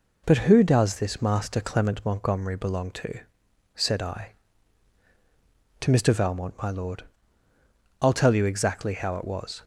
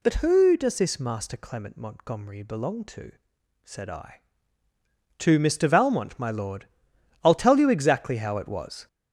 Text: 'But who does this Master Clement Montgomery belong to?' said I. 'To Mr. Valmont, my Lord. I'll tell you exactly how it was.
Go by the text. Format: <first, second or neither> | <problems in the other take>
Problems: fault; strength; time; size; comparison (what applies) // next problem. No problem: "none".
first | gets louder; noticeable; throughout; 6 dB